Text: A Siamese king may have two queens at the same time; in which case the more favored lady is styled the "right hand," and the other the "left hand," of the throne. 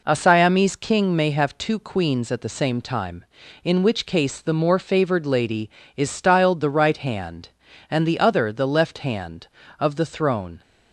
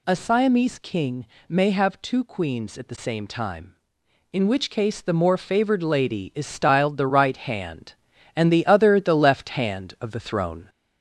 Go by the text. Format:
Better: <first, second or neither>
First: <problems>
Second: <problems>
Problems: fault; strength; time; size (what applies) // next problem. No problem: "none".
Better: first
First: none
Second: gets louder; slight; throughout; 2 dB // pauses between "king" and "may"; slight; at 1.2 s; 0.24 s long